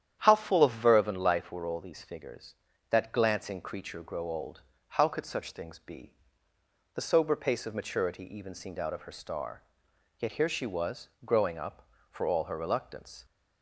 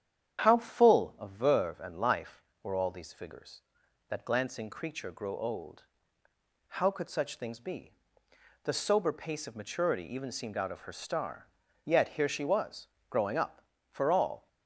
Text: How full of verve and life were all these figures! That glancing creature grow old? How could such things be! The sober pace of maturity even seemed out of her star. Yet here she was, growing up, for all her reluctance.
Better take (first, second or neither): first